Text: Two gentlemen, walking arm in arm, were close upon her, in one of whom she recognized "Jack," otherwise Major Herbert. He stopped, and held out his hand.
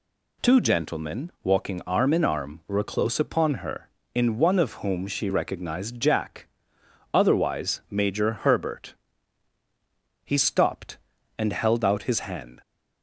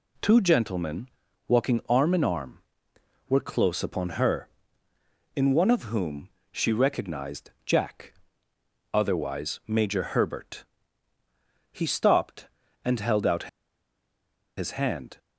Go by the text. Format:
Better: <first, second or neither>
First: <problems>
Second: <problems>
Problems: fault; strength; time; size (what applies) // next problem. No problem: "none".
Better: first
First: none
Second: pauses between "whom" and "she"; slight; at 6.3 s; 0.20 s long // pauses between "out" and "his"; at 13.4 s; 1.1 s long